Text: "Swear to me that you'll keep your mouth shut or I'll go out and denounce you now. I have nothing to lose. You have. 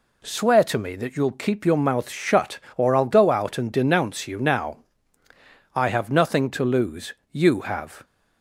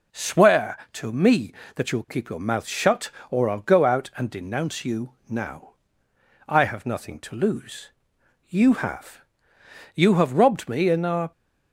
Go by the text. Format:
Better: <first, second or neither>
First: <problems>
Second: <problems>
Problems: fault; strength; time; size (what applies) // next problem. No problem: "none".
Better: first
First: none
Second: pauses between "you" and "now"; slight; at 5.1 s; 0.16 s long // goes on to say "You have robbed me in our"; from 9.9 s on; 1.3 s long